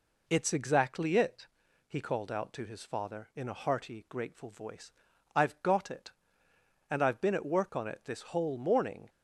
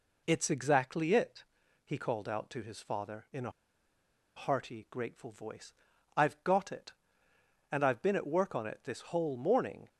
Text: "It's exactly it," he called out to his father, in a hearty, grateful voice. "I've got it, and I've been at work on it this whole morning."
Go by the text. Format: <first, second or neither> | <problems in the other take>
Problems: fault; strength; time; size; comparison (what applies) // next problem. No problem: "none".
first | pauses between "a" and "hearty"; noticeable; at 3.5 s; 0.84 s long